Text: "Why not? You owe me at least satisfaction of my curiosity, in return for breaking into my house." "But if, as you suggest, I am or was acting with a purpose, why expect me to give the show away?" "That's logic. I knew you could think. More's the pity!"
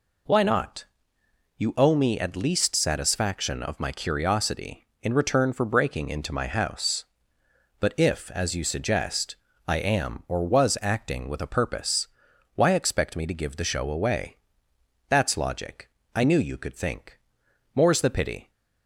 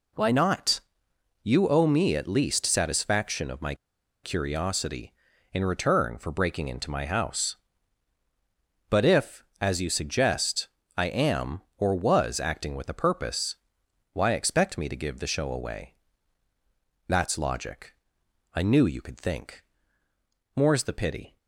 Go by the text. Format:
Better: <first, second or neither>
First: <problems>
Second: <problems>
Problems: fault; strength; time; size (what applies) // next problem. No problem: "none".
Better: first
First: none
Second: pauses between "my" and "curiosity"; noticeable; at 3.7 s; 0.49 s long